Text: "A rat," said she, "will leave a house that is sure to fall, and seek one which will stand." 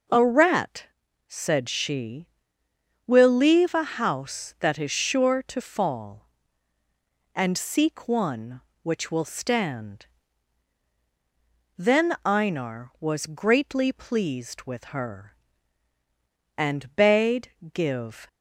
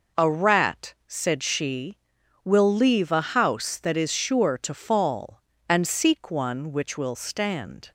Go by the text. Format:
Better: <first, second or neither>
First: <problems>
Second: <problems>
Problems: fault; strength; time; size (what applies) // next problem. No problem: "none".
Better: second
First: goes on to say "Then Einar was greatly pleased with her and bade give"; strong; from 11.7 s on; 6.5 s long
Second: none